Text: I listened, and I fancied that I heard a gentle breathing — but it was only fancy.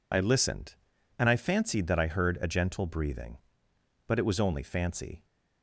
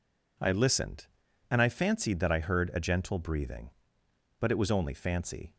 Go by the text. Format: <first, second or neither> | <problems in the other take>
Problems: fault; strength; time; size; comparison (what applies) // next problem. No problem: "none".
second | loses the start of "I"; at 0.1 s; 40 ms